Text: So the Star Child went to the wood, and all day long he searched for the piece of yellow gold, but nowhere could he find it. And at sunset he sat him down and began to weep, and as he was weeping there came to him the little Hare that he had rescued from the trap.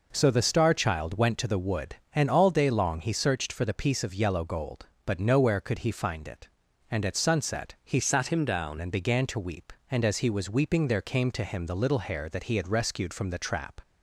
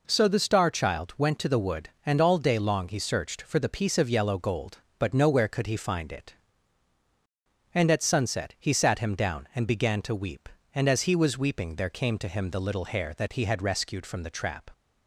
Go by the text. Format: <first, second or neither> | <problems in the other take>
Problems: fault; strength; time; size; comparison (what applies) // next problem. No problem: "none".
second | changes voice from "sat" to "down"; from 7.9 to 8.7 s; 0.8 s long